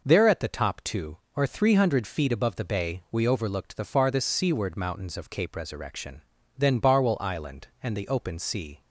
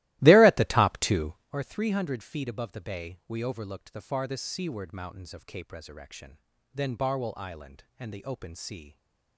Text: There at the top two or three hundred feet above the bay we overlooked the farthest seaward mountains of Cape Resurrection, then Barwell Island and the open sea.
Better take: first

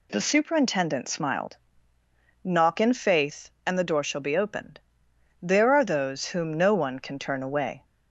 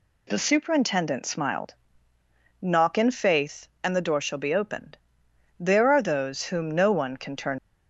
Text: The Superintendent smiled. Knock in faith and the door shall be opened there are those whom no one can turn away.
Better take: first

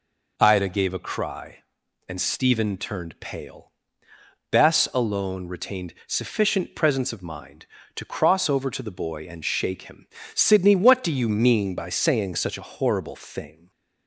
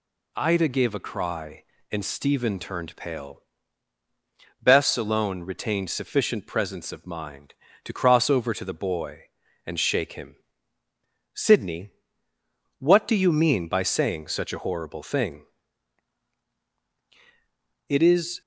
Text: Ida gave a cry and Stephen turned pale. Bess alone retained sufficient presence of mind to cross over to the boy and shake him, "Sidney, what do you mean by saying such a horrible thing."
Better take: first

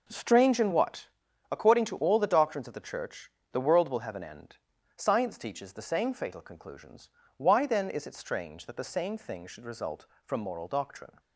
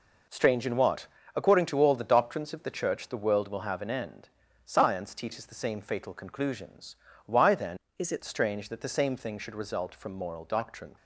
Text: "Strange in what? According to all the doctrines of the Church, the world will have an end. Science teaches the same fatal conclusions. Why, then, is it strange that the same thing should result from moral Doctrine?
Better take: first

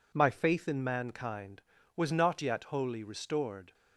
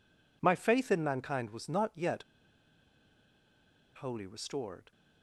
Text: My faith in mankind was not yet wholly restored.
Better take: first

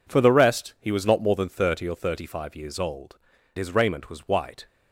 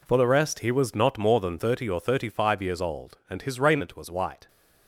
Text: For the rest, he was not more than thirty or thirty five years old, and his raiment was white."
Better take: second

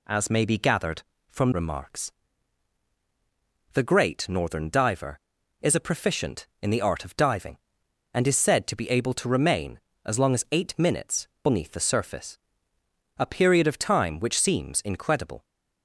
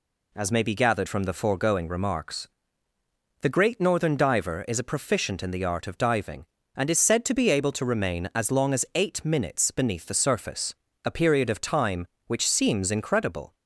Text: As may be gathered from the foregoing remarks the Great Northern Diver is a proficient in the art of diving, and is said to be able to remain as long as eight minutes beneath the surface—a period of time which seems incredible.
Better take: second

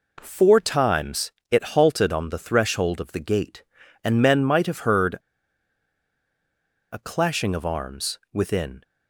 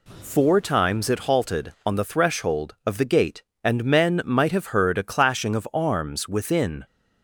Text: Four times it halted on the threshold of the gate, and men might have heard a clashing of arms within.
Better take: second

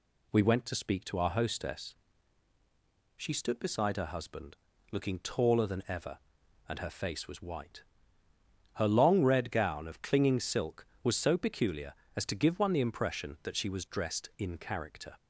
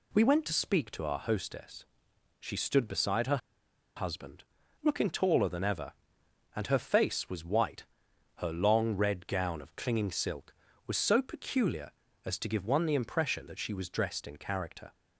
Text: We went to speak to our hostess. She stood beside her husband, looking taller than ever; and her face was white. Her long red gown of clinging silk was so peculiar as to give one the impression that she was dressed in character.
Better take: first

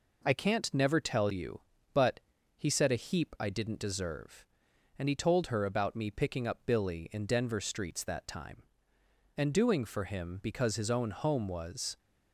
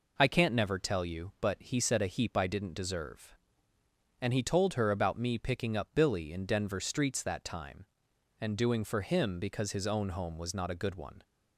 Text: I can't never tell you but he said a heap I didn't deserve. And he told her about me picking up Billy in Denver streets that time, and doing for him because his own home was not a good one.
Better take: second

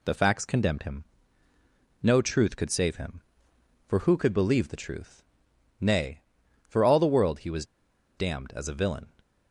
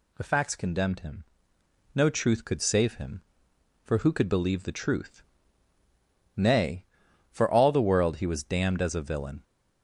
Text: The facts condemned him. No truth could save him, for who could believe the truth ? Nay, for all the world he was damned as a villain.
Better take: second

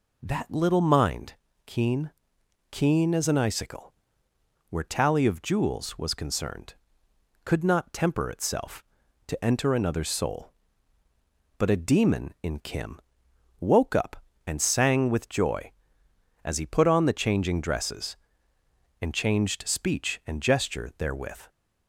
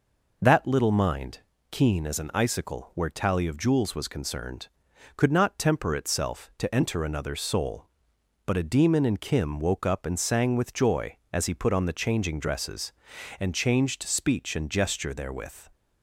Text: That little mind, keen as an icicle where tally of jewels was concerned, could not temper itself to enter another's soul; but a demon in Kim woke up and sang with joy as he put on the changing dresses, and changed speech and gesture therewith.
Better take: second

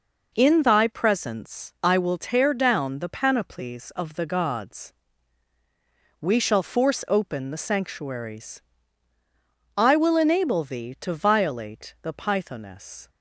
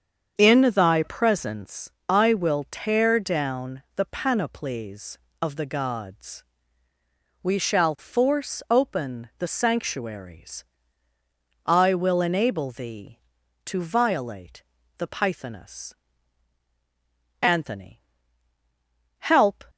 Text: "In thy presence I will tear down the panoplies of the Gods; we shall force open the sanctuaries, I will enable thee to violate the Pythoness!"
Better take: first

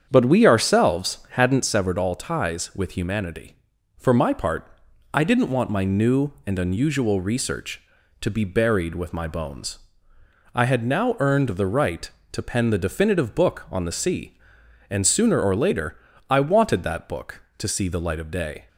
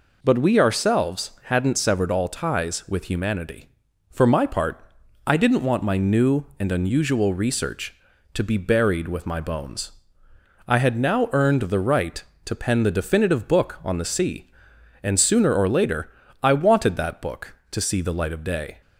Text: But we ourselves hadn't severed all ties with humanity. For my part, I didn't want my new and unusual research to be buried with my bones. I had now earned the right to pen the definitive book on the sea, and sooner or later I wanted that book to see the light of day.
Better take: second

